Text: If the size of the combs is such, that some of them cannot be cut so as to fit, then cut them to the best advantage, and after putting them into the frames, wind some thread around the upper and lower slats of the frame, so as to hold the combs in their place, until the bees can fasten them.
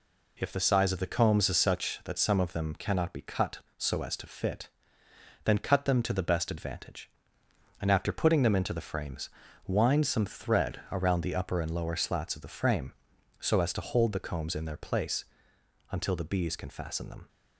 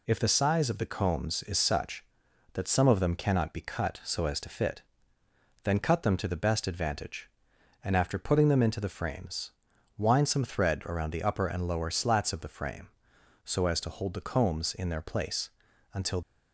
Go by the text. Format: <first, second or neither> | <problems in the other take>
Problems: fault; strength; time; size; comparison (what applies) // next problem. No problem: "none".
first | stops before "the bees can fasten them"; at 16.2 s